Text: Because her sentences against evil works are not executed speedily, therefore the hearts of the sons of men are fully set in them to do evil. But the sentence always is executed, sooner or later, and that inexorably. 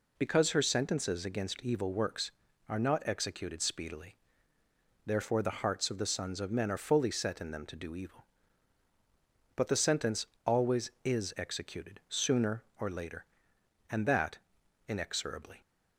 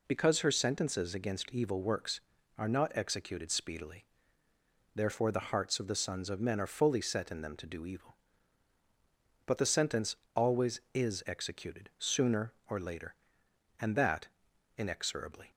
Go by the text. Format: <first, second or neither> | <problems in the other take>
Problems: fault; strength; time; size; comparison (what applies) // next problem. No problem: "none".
neither | pauses between "sentence" and "always"; slight; the same in both // pauses between "that" and "inexorably"; noticeable; the same in both